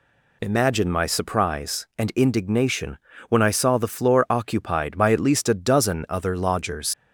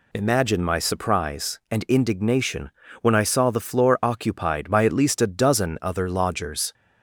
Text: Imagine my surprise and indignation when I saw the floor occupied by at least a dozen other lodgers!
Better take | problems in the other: second | pauses between "indignation" and "when"; slight; at 2.9 s; 0.30 s long; slight in the second // leaves "lodgers" unfinished; at 6.9 s; 70 ms

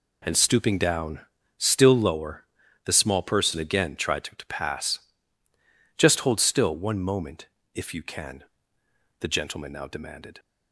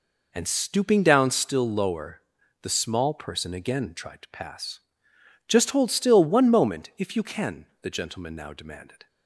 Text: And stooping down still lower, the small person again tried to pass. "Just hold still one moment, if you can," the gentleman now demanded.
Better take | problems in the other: second | pauses between "down" and "still"; at 1.1 s; 0.38 s long // says "to" twice; at 4.3 s

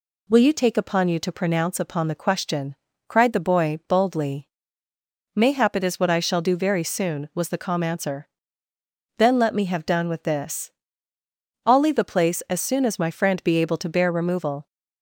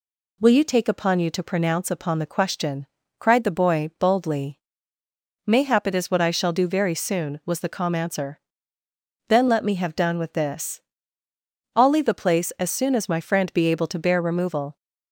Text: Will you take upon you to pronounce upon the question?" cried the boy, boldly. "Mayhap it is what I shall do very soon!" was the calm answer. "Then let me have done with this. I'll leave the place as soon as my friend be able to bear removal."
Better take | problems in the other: neither | none

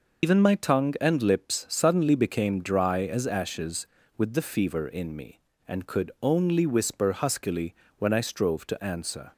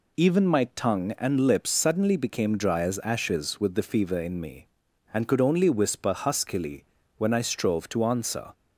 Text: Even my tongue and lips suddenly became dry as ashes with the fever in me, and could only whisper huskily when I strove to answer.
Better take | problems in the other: second | loses the start of "Even"; at 0.2 s; 80 ms // pauses between "huskily" and "when"; slight; at 7.7 s; 0.24 s long; slight in the second

